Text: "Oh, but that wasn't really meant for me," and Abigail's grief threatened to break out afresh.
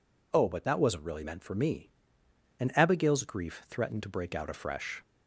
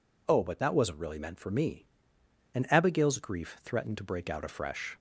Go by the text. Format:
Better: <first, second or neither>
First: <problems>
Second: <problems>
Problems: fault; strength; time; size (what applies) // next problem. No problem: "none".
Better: neither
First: none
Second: none